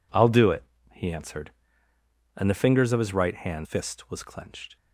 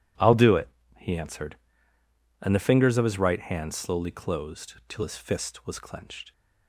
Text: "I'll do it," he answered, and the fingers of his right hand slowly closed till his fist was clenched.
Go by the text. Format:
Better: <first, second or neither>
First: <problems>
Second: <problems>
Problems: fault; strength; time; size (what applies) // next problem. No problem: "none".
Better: second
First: skips "slowly closed till his"; at 3.6 s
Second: none